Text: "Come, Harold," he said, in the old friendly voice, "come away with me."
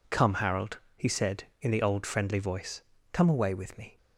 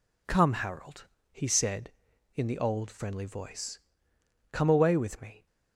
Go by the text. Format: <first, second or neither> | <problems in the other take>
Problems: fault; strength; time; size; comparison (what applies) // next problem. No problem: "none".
neither | none